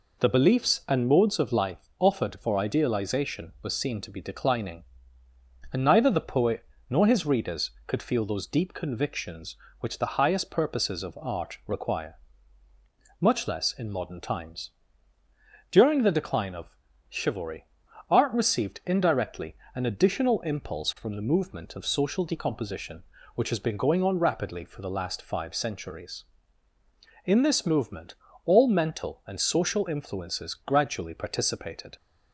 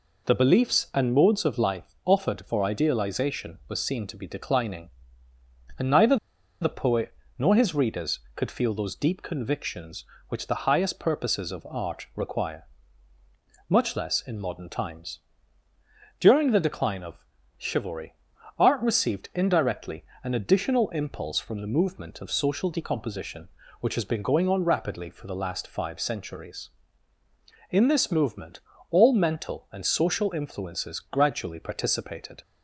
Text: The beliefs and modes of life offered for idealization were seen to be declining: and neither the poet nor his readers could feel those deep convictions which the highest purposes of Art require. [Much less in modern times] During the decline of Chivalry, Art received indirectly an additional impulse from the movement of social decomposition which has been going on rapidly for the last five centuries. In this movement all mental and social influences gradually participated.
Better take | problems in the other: first | pauses between "neither" and "the"; at 6.1 s; 0.45 s long // pauses between "poet" and "nor"; slight; at 7.1 s; 0.26 s long; slight in the first // pauses between "times" and "During"; at 15.1 s; 1.0 s long; also in the first // pauses between "of" and "Chivalry"; slight; at 17.2 s; 0.34 s long; slight in the first // pauses between "indirectly" and "an"; slight; at 20.0 s; 0.22 s long; slight in the first // pauses between "movement" and "all"; slight; at 28.5 s; 0.30 s long; slight in the first

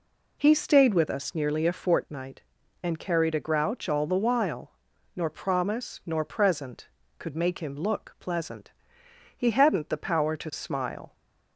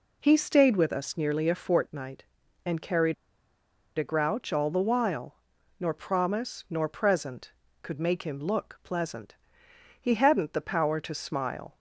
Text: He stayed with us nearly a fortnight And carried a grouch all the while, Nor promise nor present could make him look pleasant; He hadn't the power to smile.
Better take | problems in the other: first | pauses between "carried" and "a"; noticeable; at 3.1 s; 0.83 s long

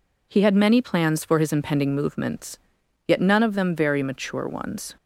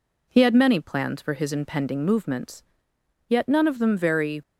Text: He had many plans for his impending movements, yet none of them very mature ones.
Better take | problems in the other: first | stops before "mature ones"; at 4.4 s

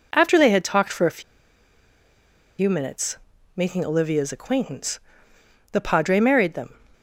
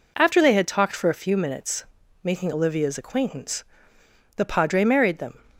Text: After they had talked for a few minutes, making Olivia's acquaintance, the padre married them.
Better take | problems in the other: second | pauses between "a" and "few"; strong; at 1.2 s; 1.3 s long

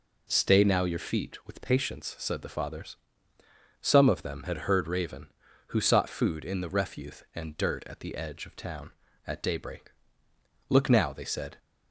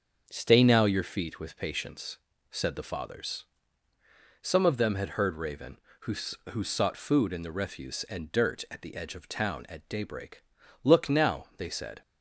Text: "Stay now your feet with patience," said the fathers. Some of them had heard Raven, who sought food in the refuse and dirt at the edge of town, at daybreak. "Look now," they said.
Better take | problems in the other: first | starts louder than the rest; until 1.3 s; 7 dB // says "who" twice; at 6.4 s

